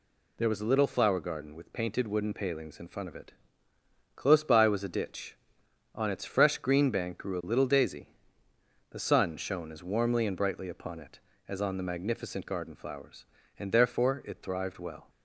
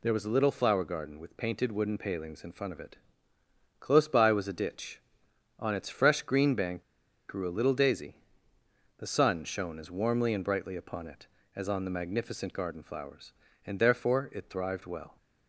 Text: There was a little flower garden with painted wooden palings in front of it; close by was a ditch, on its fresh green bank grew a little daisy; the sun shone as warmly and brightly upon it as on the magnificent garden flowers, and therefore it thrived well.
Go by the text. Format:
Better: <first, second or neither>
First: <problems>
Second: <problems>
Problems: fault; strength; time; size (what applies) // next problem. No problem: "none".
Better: first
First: none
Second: pauses between "bank" and "grew"; noticeable; at 6.8 s; 0.47 s long